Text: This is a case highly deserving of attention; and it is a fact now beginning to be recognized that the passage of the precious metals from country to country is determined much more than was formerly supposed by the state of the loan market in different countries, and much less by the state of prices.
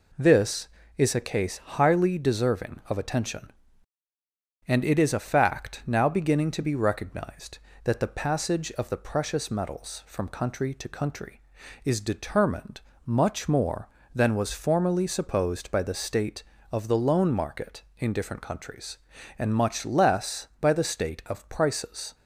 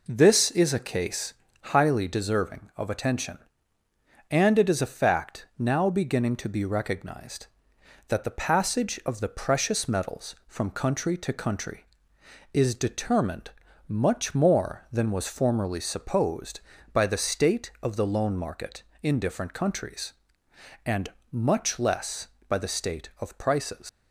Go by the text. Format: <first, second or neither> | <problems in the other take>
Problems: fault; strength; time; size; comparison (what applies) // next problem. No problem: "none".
first | pauses between "case" and "highly"; at 1.3 s; 0.38 s long // pauses between "determined" and "much"; at 13.4 s; 0.38 s long; slight in the first // pauses between "and" and "much"; slight; at 21.0 s; 0.22 s long // leaves "prices" unfinished; at 23.8 s; 110 ms